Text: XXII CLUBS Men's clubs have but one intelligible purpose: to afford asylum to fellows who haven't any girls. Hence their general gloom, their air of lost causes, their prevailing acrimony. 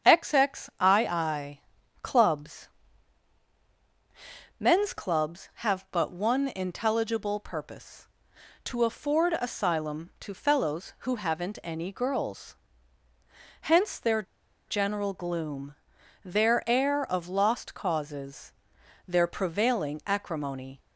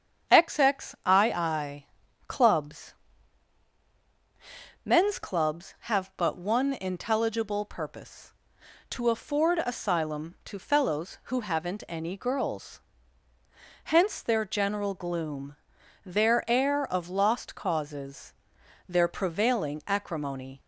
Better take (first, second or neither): second